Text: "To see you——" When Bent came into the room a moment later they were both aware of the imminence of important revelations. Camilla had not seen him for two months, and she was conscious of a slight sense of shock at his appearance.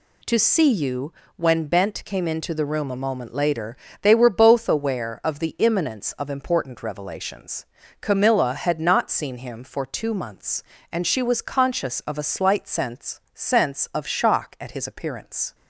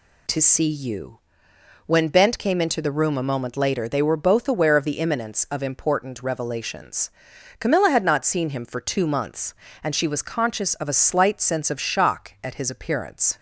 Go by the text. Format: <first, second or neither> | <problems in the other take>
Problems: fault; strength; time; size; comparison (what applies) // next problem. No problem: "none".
second | pauses between "later" and "they"; slight; at 3.7 s; 0.28 s long // says "sense" twice; at 13.3 s